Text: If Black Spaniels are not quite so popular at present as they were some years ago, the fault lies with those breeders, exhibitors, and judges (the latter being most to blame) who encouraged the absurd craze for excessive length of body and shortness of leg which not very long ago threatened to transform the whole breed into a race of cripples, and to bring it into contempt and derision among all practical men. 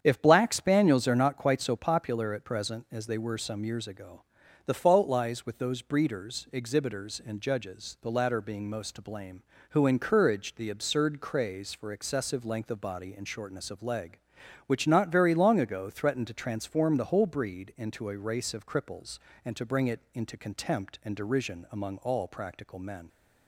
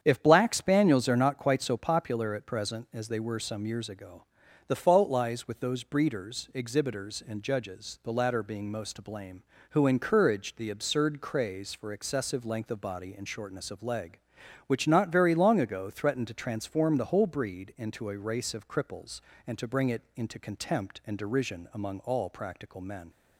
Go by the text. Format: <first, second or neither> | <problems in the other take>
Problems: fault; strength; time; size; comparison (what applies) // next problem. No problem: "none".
neither | starts louder than the rest; strong; the same in both // pauses between "it" and "into"; slight; the same in both